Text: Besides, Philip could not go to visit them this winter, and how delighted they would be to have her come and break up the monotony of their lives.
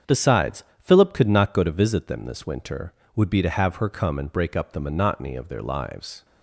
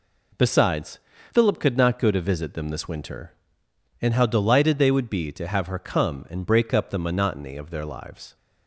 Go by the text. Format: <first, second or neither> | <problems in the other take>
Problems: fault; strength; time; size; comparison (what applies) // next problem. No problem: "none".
second | starts louder than the rest; strong; until 1.2 s; 7.5 dB // skips "and how delighted they"; at 3.0 s